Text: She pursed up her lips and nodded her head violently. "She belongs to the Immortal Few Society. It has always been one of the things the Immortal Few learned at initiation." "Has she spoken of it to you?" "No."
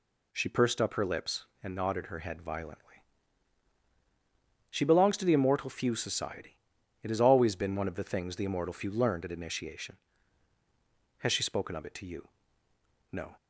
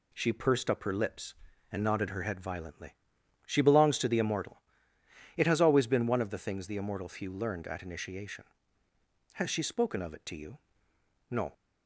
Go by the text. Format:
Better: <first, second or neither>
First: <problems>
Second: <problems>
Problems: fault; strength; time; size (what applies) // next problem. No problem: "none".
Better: first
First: none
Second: skips "Few Society"; at 4.9 s